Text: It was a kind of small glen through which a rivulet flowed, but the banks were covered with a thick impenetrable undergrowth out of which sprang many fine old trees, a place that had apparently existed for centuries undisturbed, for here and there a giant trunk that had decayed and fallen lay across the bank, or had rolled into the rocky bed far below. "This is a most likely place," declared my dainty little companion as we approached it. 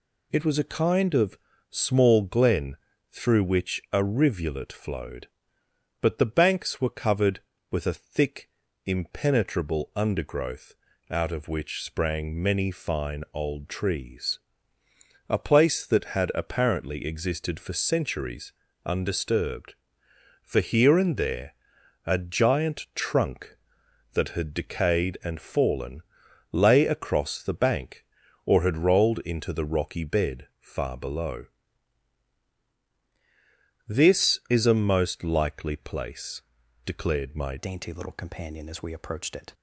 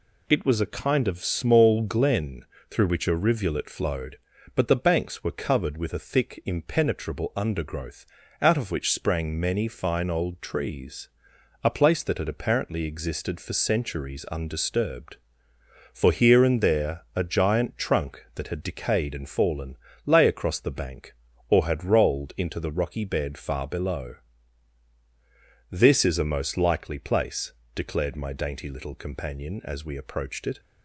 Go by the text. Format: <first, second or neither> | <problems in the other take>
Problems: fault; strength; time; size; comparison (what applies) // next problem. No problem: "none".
second | pauses between "of" and "small"; slight; at 1.3 s; 0.34 s long // pauses between "glen" and "through"; slight; at 2.7 s; 0.34 s long; slight in the second // pauses between "thick" and "impenetrable"; at 8.4 s; 0.38 s long // pauses between "undergrowth" and "out"; slight; at 10.7 s; 0.36 s long; slight in the second // pauses between "centuries" and "undisturbed"; slight; at 18.5 s; 0.32 s long // pauses between "there" and "a"; noticeable; at 21.5 s; 0.54 s long // pauses between "fallen" and "lay"; noticeable; at 26.0 s; 0.52 s long; slight in the second // changes voice at "dainty"; from 37.5 s on; 2.0 s long